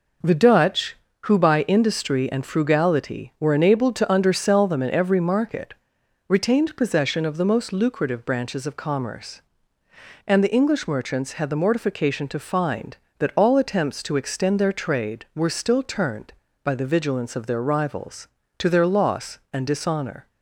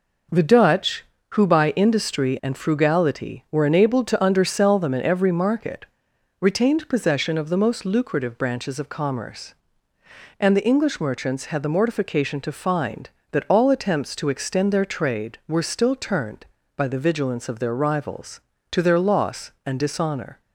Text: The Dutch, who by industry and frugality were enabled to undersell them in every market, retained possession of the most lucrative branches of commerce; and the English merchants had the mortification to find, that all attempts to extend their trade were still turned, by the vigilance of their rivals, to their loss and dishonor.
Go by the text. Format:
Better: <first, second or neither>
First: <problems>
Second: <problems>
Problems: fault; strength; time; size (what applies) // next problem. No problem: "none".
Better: neither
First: none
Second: none